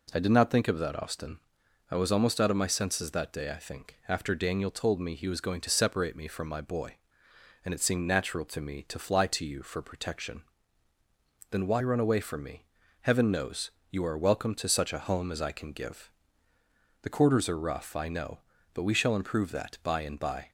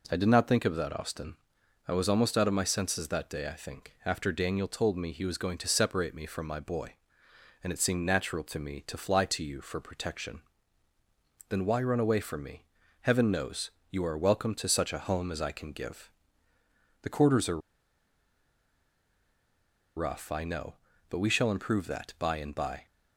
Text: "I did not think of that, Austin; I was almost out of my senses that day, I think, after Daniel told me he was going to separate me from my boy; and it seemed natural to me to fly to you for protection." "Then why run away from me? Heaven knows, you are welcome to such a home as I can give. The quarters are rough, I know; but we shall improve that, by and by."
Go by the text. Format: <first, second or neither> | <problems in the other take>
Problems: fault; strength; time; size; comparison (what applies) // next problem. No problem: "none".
first | pauses between "are" and "rough"; strong; at 17.5 s; 2.3 s long